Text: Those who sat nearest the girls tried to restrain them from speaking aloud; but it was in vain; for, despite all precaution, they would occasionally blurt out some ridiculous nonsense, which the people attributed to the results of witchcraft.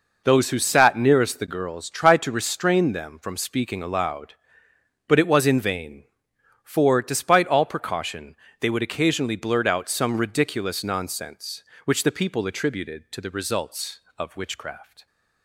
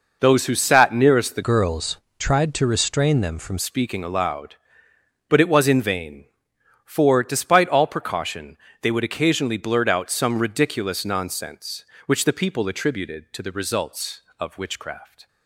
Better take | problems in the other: first | changes voice from "girls" to "from"; from 1.4 to 3.5 s; 2.1 s long // pauses between "girls" and "tried"; slight; at 1.9 s; 0.22 s long

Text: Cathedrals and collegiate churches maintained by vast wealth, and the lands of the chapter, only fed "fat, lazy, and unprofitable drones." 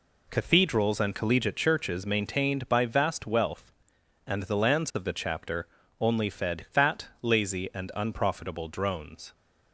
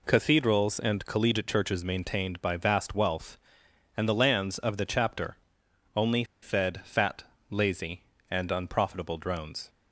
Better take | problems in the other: first | pauses between "only" and "fed"; slight; at 6.2 s; 0.16 s long

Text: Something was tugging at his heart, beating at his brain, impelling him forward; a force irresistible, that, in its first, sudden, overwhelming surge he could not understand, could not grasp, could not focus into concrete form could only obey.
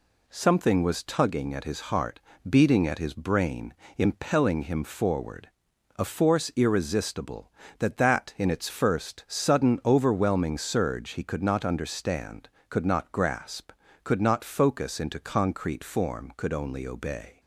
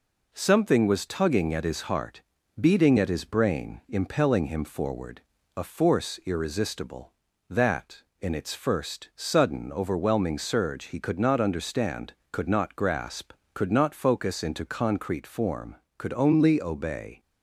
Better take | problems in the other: second | says "that" twice; at 7.9 s

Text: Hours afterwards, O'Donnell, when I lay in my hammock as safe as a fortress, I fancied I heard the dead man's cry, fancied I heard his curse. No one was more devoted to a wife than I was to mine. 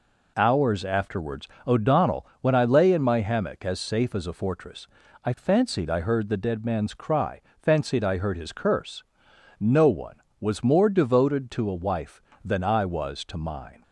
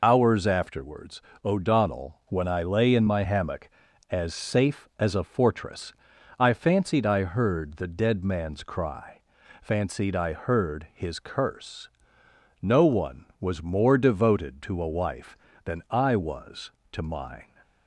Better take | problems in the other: first | loses the start of "Hours"; at 0.0 s; 65 ms

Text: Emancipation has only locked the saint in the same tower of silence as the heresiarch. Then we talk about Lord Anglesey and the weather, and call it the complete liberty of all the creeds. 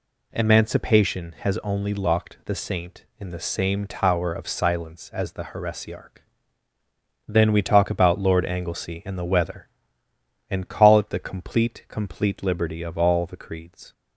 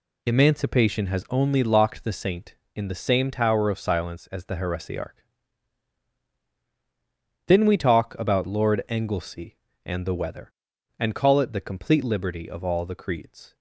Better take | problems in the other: second | says "complete" twice; at 11.8 s

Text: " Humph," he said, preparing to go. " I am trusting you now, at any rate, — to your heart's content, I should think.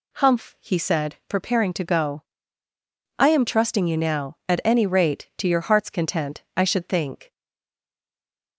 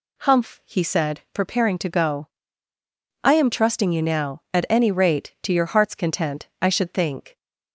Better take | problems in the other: second | stays silent after the last word; noticeable; from 7.3 s on; 1.2 s long

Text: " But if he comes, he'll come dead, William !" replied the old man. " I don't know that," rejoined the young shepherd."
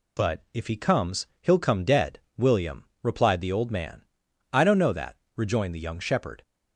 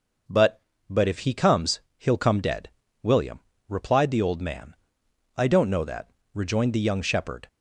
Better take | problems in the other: first | starts louder than the rest; until 1.5 s; 6 dB // says "But" twice; at 0.8 s

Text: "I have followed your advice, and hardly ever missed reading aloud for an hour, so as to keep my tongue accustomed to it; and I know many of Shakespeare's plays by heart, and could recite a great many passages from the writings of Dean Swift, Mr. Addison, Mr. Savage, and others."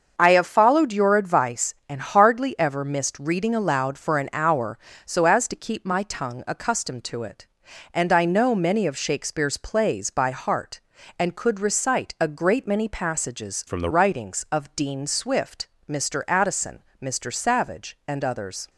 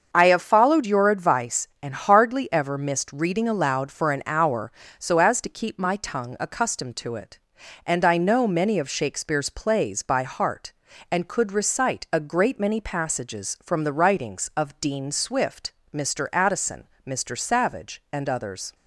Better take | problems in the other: second | starts louder than the rest; until 1.2 s; 6.5 dB; also in the second // changes voice from "from" to "the"; from 13.6 to 13.9 s; 0.3 s long

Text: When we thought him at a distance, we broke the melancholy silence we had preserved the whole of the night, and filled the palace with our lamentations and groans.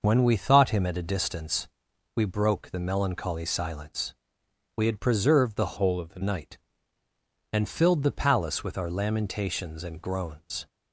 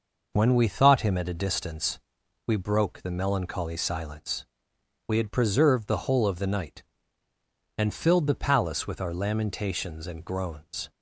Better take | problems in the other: second | pauses between "silence" and "we"; noticeable; at 4.1 s; 0.62 s long; noticeable in the second // changes voice from "whole" to "the"; from 5.7 to 6.1 s; 0.4 s long

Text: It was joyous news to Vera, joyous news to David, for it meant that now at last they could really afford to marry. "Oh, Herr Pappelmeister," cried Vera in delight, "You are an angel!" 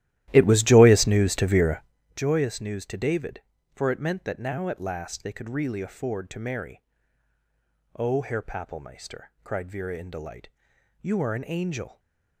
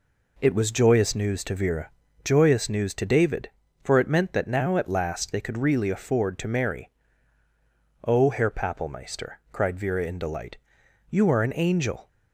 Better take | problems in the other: second | starts louder than the rest; strong; until 1.9 s; 14.5 dB

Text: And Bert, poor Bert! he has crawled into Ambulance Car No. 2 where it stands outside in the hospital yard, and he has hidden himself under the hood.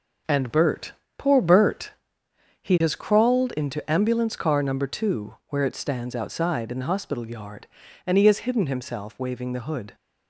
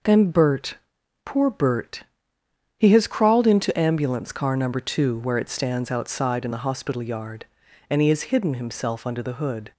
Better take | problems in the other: second | says "waving" for "under"; at 9.1 s

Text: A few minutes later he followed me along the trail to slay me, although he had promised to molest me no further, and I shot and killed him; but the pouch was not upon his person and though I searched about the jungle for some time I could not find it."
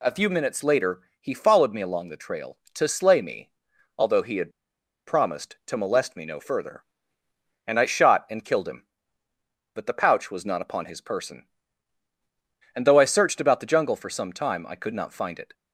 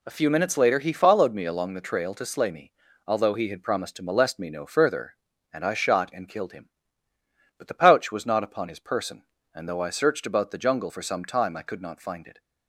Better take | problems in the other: second | pauses between "later" and "he"; slight; at 1.0 s; 0.18 s long // pauses between "had" and "promised"; noticeable; at 4.5 s; 0.56 s long

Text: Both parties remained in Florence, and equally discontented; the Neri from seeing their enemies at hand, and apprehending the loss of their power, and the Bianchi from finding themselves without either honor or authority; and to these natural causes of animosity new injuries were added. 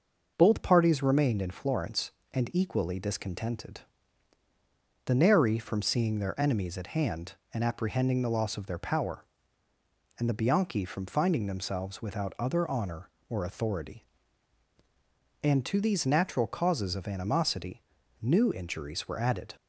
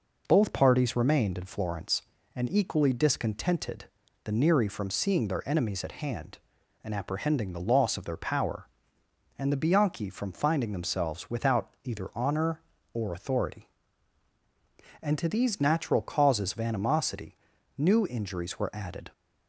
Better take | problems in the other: second | says "other" for "either"; at 12.3 s // pauses between "animosity" and "new"; at 17.8 s; 0.40 s long; also in the second

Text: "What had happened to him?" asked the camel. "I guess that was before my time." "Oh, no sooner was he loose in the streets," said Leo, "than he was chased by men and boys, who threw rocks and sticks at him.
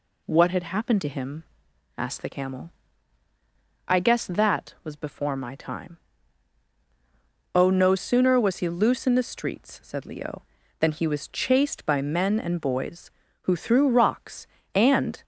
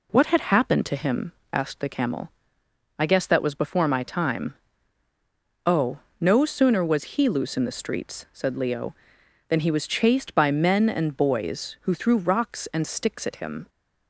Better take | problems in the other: second | stops before "sticks at him"; at 15.2 s

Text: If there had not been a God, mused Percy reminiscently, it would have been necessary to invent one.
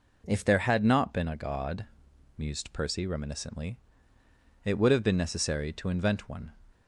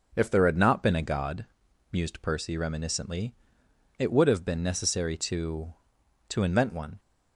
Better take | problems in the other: first | says "to" twice; at 6.2 s

